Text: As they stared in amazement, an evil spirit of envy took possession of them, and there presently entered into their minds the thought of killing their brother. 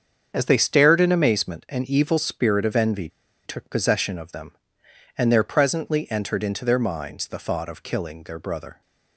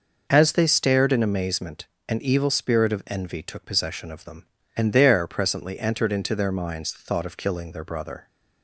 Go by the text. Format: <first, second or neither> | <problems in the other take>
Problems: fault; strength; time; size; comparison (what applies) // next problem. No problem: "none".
second | starts louder than the rest; strong; until 1.3 s; 7 dB // pauses between "envy" and "took"; at 3.0 s; 0.37 s long